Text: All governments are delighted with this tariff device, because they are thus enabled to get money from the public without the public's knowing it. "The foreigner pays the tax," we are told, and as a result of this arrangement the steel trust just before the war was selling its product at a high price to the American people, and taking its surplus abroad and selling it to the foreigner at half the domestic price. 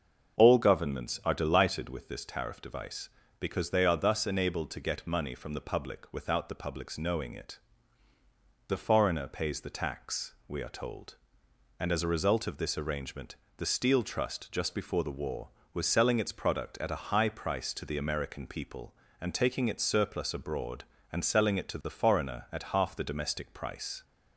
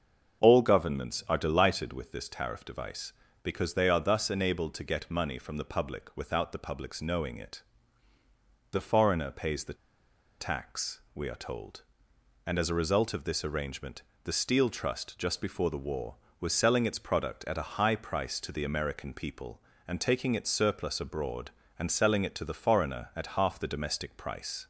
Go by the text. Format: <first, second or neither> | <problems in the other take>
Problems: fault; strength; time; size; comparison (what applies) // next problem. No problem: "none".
first | starts louder than the rest; until 1.4 s; 6.5 dB; also in the first // pauses between "the" and "tax"; noticeable; at 9.7 s; 0.65 s long // pauses between "arrangement" and "the"; slight; at 14.0 s; 0.22 s long; slight in the first